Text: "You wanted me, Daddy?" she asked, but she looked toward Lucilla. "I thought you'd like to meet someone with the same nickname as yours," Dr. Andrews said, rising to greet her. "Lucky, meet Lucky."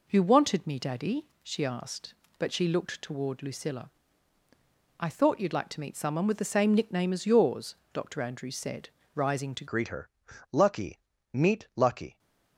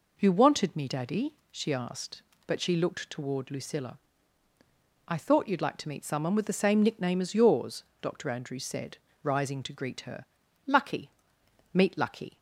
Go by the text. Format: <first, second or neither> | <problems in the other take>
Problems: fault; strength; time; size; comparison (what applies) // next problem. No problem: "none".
second | changes voice at "greet"; from 9.6 s on; 2.5 s long